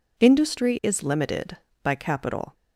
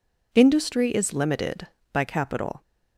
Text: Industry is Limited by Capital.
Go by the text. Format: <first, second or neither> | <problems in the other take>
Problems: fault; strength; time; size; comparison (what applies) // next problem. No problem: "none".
neither | none